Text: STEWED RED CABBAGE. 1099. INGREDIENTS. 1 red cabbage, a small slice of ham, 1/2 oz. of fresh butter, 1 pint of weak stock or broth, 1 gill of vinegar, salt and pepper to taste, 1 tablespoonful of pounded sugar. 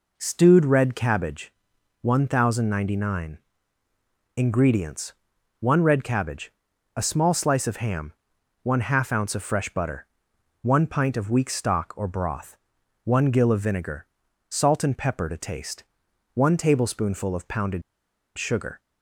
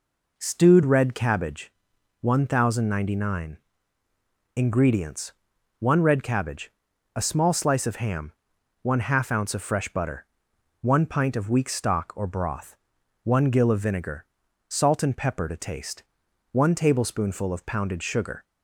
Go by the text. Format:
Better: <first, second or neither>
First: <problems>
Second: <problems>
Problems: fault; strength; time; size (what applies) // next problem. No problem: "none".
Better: second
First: pauses between "pounded" and "sugar"; noticeable; at 17.8 s; 0.55 s long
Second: none